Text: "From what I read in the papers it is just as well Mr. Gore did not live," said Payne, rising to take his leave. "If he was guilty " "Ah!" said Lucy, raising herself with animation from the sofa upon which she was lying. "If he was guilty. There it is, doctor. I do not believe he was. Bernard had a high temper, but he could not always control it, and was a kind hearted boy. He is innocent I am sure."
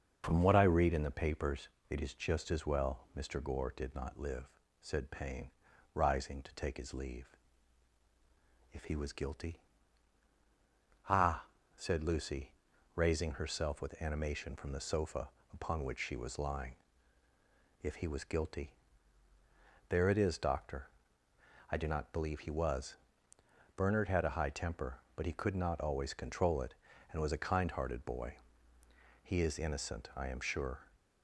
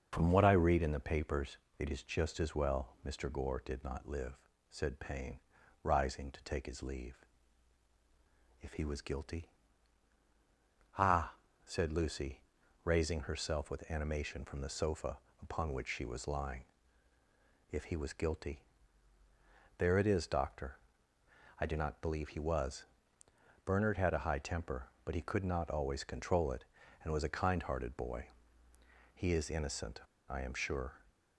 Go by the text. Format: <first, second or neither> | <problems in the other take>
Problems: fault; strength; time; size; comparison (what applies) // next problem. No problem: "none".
first | starts louder than the rest; until 1.1 s; 7 dB; also in the first // pauses between "papers" and "it"; slight; at 1.5 s; 0.22 s long; slight in the first // pauses between "sofa" and "upon"; slight; at 15.1 s; 0.24 s long; slight in the first // pauses between "innocent" and "I"; slight; at 30.0 s; 0.26 s long